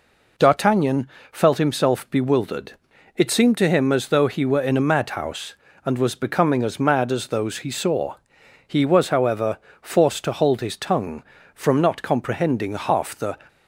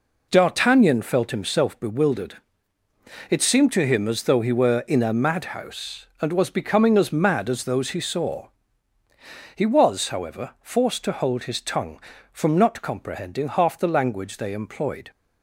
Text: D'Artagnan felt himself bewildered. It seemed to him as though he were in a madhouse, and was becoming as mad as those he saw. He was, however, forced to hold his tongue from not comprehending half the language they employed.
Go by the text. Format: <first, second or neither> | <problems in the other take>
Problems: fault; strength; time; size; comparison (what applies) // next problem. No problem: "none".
second | pauses between "D'Artagnan" and "felt"; slight; at 1.0 s; 0.22 s long // stops before "language they employed"; at 13.4 s